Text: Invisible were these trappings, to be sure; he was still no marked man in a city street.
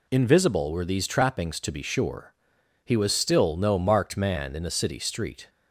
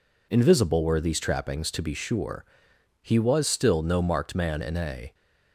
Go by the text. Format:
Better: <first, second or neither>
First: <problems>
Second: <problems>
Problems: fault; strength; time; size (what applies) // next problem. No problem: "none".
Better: first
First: none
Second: stops before "city street"; at 5.1 s